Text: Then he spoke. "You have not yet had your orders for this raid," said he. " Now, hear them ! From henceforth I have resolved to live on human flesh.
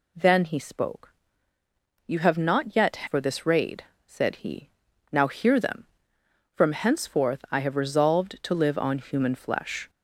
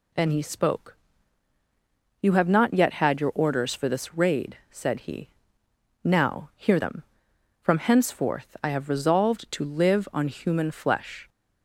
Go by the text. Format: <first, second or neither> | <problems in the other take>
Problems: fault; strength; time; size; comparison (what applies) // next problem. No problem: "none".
second | skips "had your orders"; at 3.0 s